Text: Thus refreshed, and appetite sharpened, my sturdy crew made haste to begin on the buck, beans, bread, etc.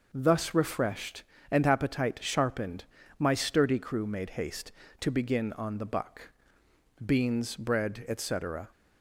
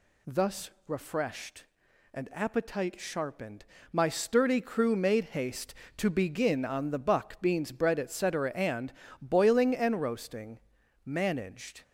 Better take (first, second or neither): first